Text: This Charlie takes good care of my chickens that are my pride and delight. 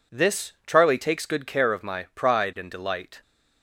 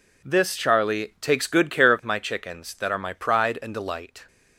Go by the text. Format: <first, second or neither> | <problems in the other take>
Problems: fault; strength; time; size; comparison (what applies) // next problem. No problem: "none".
second | skips "my chickens that are"; at 1.8 s